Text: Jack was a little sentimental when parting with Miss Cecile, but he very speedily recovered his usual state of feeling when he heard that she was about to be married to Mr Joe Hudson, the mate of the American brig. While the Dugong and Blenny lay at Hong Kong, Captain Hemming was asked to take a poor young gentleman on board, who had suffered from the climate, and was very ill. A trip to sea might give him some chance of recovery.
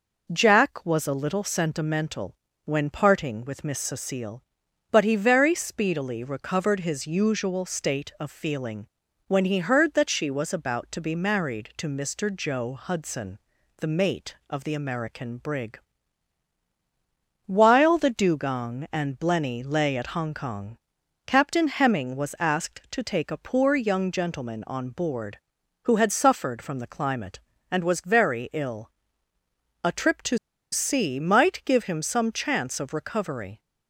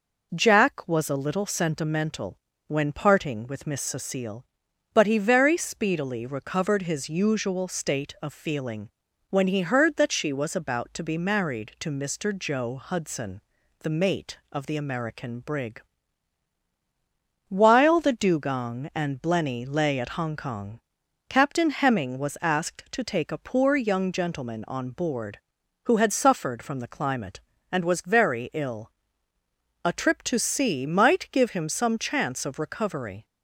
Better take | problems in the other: second | pauses between "sentimental" and "when"; slight; at 2.3 s; 0.30 s long; slight in the second // pauses between "feeling" and "when"; at 8.8 s; 0.40 s long; also in the second // pauses between "to" and "sea"; slight; at 30.3 s; 0.34 s long

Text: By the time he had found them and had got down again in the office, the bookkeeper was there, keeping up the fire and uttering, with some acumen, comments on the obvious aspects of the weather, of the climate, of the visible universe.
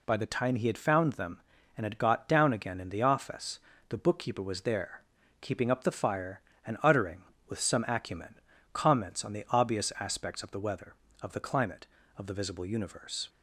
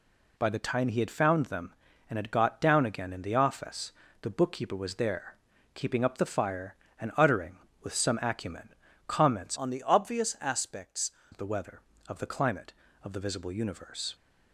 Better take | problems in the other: first | changes voice from "on" to "aspects"; from 9.5 to 11.1 s; 1.6 s long

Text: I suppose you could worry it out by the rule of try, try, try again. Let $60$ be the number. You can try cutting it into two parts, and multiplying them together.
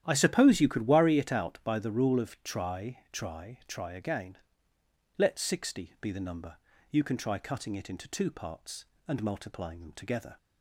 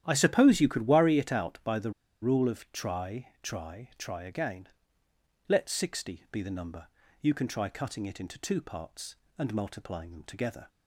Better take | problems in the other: first | starts louder than the rest; strong; until 1.0 s; 11 dB; strong in the first // pauses between "the" and "rule"; slight; at 1.9 s; 0.30 s long

